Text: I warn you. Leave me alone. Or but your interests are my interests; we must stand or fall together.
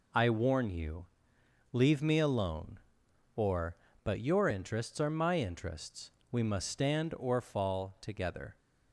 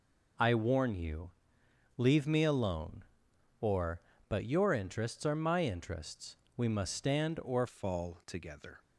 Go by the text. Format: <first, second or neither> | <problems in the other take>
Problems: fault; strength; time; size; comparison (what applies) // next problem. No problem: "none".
first | changes voice at "fall"; from 7.6 s on; 1.2 s long